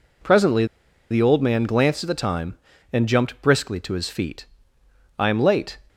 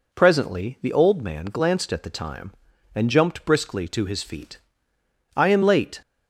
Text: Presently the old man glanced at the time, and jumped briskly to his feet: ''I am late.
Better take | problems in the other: second | pauses between "Presently" and "the"; noticeable; at 0.6 s; 0.46 s long

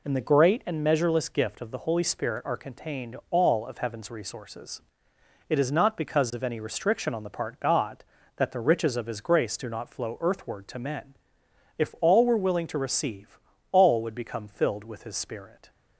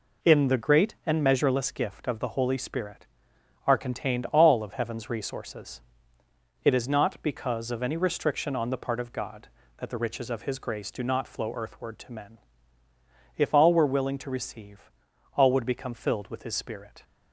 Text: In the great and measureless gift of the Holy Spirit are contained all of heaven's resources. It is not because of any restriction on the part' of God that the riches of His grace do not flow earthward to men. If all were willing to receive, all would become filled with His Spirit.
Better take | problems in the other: neither | none

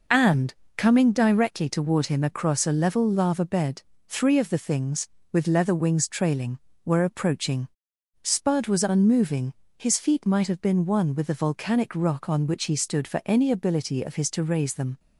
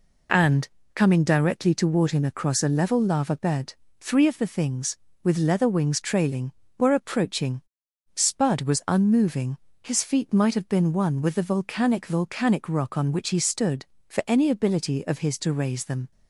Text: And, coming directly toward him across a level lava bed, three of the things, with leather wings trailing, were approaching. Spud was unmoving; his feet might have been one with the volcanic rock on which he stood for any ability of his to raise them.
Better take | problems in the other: first | says "volcanic" twice; at 12.0 s

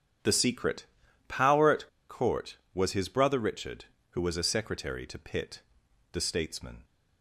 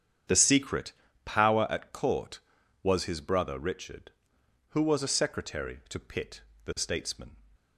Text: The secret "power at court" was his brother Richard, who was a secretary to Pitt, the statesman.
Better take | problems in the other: second | starts louder than the rest; strong; until 1.6 s; 8.5 dB; strong in the second // pauses between "secret" and "power"; at 0.8 s; 0.44 s long; slight in the second // pauses between "at" and "court"; slight; at 1.8 s; 0.21 s long

